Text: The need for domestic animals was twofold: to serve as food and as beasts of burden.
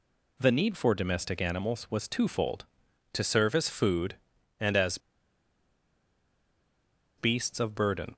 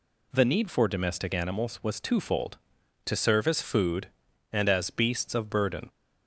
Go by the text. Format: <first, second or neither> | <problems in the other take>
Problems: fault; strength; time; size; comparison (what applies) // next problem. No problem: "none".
second | pauses between "as" and "beasts"; strong; at 4.9 s; 2.1 s long